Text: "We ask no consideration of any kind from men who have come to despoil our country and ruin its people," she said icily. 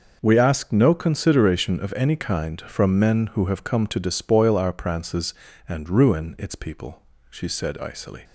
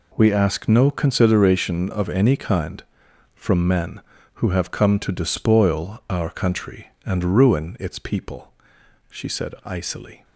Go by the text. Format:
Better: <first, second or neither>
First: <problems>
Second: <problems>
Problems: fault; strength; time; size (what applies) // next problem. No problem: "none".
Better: second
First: says "prances" for "country"; at 4.7 s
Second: none